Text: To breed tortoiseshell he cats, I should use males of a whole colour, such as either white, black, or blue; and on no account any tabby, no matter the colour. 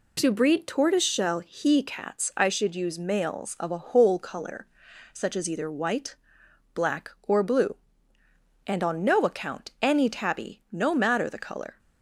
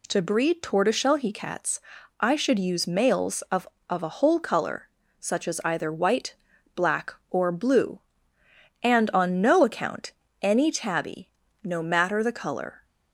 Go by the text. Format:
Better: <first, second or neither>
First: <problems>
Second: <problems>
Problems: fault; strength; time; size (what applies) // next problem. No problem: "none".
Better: first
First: none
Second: says "of" twice; at 3.8 s // pauses between "account" and "any"; slight; at 10.1 s; 0.30 s long